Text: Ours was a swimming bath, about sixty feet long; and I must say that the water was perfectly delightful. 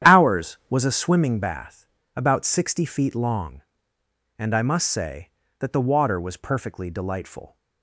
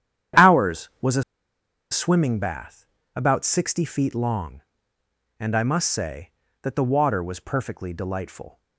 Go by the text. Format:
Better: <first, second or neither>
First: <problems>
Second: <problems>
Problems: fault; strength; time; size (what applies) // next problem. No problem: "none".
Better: first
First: starts louder than the rest; strong; until 1.1 s; 10 dB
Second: starts louder than the rest; strong; until 2.1 s; 10 dB // pauses between "a" and "swimming"; noticeable; at 1.2 s; 0.68 s long